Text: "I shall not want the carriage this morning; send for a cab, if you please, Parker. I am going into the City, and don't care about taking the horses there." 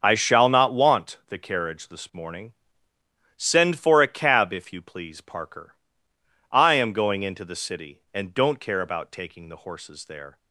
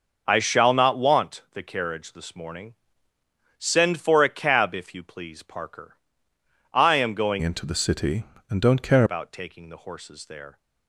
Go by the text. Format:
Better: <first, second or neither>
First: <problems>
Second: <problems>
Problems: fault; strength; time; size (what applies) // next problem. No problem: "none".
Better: first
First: starts louder than the rest; until 1.0 s; 7 dB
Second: starts louder than the rest; until 1.2 s; 6.5 dB // changes voice from "into" to "care"; from 7.3 to 9.0 s; 1.7 s long